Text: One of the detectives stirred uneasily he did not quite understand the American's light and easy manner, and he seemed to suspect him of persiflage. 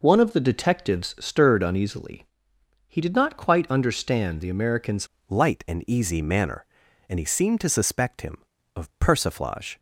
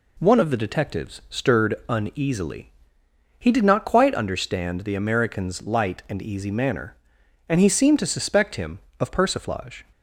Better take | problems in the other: second | pauses between "uneasily" and "he"; noticeable; at 2.2 s; 0.64 s long; noticeable in the second // changes voice at "light"; from 5.2 s on; 4.5 s long

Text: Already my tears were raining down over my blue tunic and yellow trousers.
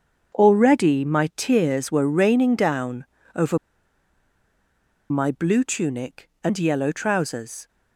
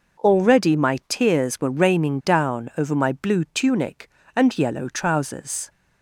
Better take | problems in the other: second | starts louder than the rest; until 1.4 s; 7 dB // pauses between "down" and "over"; slight; at 3.0 s; 0.30 s long // pauses between "over" and "my"; strong; at 3.5 s; 1.5 s long

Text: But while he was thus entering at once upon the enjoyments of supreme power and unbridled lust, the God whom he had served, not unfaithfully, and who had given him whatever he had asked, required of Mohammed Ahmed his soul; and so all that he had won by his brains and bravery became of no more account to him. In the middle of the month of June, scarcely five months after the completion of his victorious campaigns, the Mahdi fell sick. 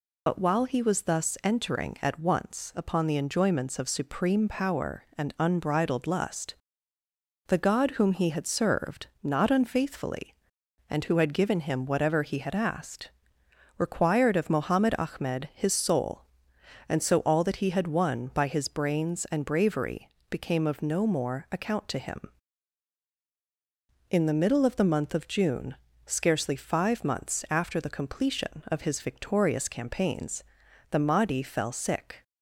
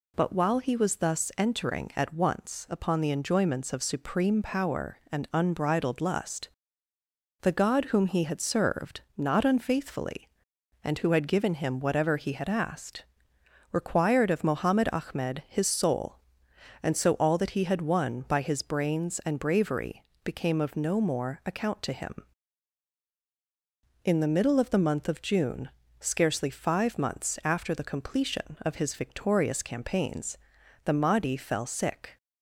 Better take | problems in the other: second | loses the start of "But"; at 0.2 s; 55 ms // pauses between "bravery" and "became"; slight; at 20.0 s; 0.20 s long; slight in the second

